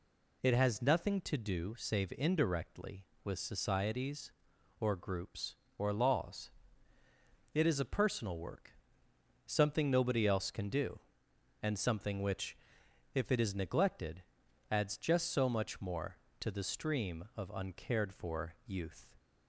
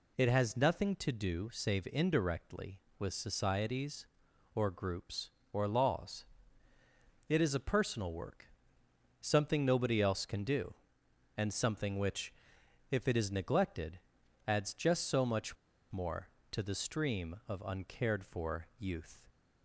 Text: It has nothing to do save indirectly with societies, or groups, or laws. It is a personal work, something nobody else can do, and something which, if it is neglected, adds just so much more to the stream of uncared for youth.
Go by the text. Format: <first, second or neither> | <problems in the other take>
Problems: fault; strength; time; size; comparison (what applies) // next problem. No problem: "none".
first | pauses between "much" and "more"; slight; at 15.5 s; 0.35 s long